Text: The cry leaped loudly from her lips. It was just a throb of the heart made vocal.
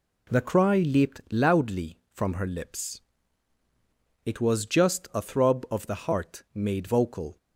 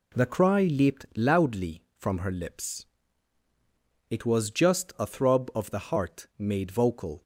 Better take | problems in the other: neither | none

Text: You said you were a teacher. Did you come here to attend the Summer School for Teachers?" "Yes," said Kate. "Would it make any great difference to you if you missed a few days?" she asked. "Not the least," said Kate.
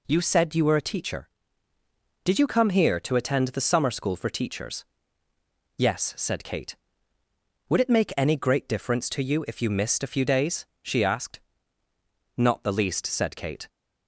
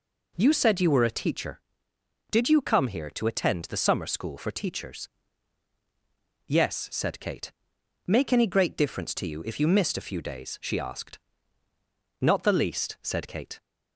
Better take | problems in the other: first | skips "Would it"; at 7.7 s

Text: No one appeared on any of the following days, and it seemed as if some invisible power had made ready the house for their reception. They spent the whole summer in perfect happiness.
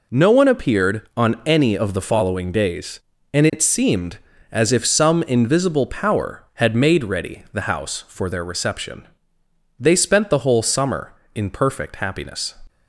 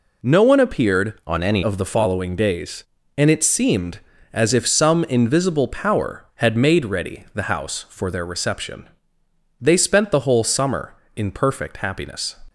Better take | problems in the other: first | changes voice from "on" to "any"; from 1.2 to 1.6 s; 0.4 s long

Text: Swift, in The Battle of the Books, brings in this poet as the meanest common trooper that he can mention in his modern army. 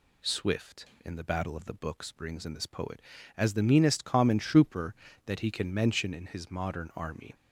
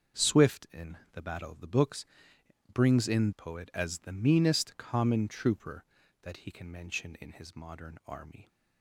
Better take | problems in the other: first | starts louder than the rest; until 1.4 s; 6.5 dB // pauses between "in" and "The"; slight; at 0.9 s; 0.16 s long // skips "this"; at 3.3 s

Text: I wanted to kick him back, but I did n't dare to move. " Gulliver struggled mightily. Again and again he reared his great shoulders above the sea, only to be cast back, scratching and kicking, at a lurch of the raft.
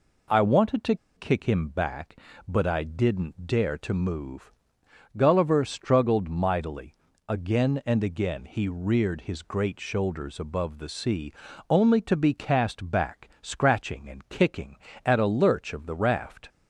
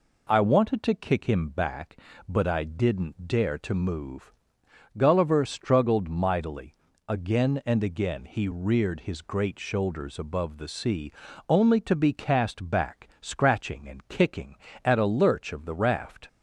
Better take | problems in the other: second | pauses between "to" and "kick"; slight; at 0.9 s; 0.21 s long

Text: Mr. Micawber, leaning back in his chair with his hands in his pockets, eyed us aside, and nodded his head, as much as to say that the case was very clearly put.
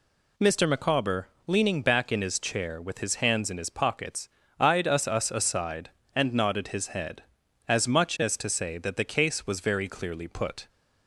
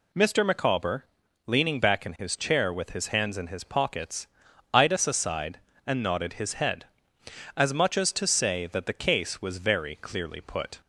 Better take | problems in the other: second | says "us" twice; at 5.0 s

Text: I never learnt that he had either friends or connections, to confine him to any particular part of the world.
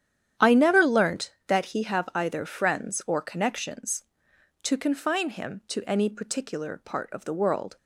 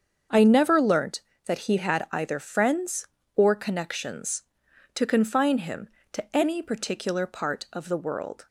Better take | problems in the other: second | starts louder than the rest; strong; until 1.5 s; 9.5 dB; also in the second // says "have" for "had"; at 1.8 s

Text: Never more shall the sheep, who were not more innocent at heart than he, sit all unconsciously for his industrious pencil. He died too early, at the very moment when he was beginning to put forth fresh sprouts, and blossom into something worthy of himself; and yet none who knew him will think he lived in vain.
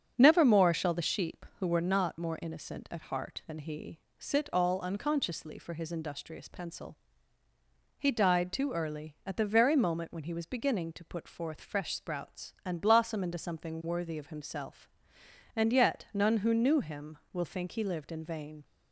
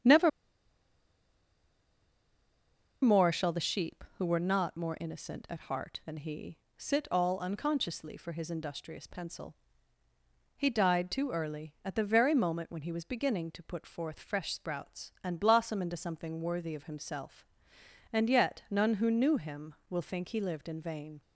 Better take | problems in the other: first | starts louder than the rest; until 3.7 s; 7 dB; also in the first // pauses between "Never" and "more"; strong; at 0.2 s; 2.7 s long

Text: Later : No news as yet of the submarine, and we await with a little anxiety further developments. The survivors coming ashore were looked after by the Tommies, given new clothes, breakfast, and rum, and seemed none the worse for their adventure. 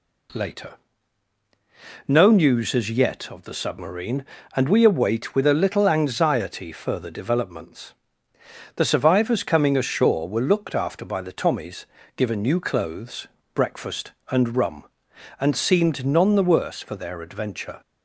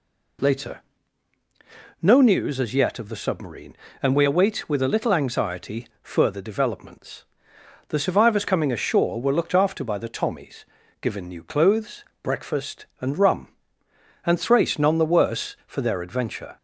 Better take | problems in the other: first | pauses between "anxiety" and "further"; slight; at 5.8 s; 0.16 s long // says "thrace" for "seemed"; at 14.3 s

